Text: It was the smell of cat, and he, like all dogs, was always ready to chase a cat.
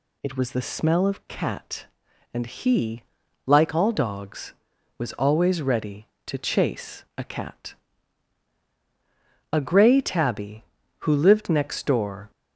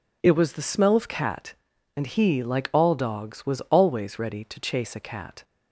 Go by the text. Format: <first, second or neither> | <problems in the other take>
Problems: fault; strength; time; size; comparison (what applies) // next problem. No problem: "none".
second | goes on to say "A gray tabby who lived next door"; strong; from 9.5 s on; 2.7 s long